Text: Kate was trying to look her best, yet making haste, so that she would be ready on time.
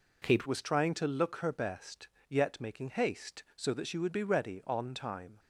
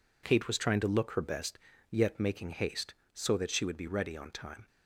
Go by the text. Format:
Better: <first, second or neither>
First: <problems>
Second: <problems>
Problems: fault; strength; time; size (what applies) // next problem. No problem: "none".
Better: second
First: changes voice at "was"; from 0.4 s on; 4.9 s long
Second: none